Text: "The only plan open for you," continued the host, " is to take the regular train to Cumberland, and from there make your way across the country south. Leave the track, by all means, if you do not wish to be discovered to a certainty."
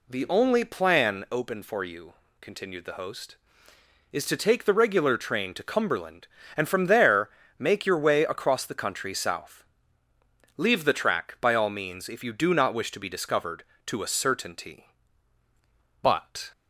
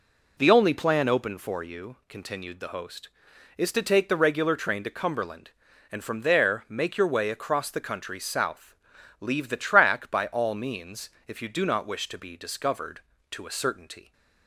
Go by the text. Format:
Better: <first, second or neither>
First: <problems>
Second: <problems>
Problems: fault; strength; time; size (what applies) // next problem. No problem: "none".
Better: second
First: pauses between "there" and "make"; slight; at 7.2 s; 0.28 s long // goes on to say "But"; from 16.0 s on; 0.50 s long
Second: none